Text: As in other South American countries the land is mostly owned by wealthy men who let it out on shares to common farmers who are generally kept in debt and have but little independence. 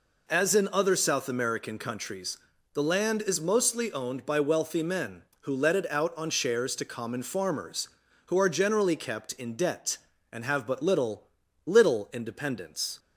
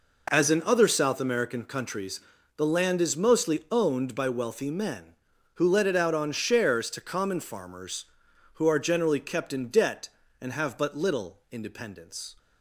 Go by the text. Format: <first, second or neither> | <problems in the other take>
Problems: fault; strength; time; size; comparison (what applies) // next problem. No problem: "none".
second | pauses between "countries" and "the"; slight; at 2.3 s; 0.34 s long; slight in the second // says "little" twice; at 11.6 s